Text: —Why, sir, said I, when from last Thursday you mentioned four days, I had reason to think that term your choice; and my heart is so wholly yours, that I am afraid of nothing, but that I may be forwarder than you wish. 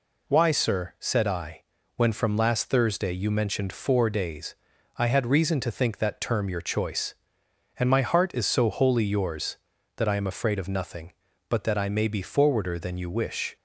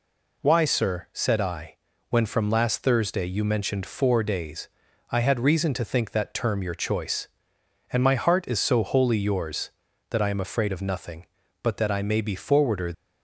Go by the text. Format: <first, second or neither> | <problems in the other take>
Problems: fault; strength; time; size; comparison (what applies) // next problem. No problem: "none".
first | stops before "than you wish"; at 12.9 s